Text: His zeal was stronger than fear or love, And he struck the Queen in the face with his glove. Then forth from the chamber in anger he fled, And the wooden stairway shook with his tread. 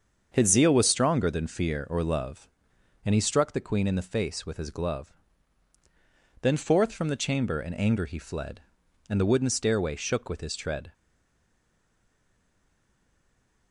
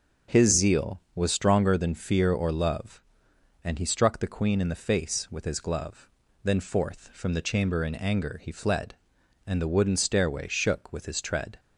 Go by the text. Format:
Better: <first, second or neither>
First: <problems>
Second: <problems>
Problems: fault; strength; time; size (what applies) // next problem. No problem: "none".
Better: second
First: starts louder than the rest; until 1.3 s; 7 dB // stays silent after the last word; strong; from 10.9 s on; 2.8 s long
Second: none